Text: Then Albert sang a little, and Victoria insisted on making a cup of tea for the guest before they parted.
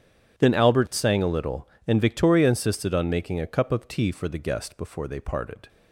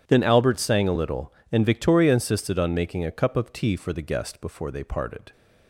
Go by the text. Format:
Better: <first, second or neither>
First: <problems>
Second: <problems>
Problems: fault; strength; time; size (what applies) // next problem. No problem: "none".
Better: neither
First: starts louder than the rest; strong; until 1.4 s; 10.5 dB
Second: starts louder than the rest; strong; until 1.1 s; 10 dB